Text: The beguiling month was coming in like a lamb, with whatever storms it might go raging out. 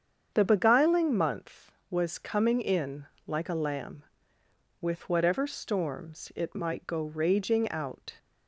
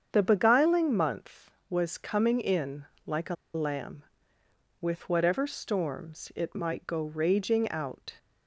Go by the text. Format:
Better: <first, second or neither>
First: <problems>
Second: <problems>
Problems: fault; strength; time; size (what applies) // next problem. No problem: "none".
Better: first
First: starts louder than the rest; strong; until 1.3 s; 7.5 dB // pauses between "in" and "like"; slight; at 3.0 s; 0.20 s long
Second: starts louder than the rest; strong; until 1.1 s; 7.5 dB // pauses between "in" and "like"; slight; at 2.8 s; 0.20 s long // pauses between "a" and "lamb"; slight; at 3.3 s; 0.19 s long